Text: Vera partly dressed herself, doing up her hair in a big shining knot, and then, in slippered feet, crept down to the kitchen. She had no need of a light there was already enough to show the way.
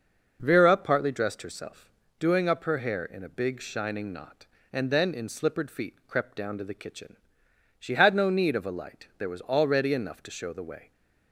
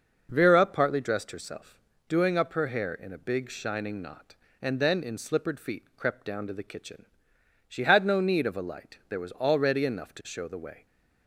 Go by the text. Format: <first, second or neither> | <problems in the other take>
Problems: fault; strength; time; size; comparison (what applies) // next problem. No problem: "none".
neither | none